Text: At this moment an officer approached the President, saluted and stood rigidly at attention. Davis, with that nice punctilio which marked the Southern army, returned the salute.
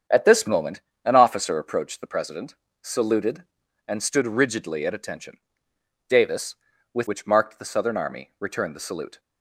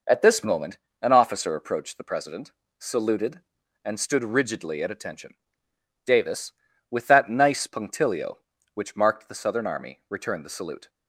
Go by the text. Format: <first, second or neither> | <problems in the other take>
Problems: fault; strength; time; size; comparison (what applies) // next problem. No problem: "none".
second | starts louder than the rest; strong; until 1.3 s; 8 dB // pauses between "moment" and "an"; slight; at 0.8 s; 0.22 s long; slight in the second // skips "that nice punctilio"; at 7.0 s